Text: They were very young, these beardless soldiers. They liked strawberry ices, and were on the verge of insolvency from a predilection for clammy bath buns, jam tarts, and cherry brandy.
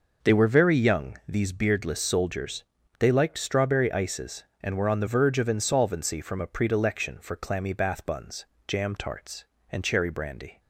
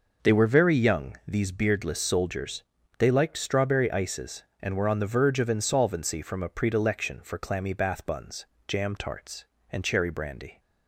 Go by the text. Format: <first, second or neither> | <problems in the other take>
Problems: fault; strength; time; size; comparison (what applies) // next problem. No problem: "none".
neither | none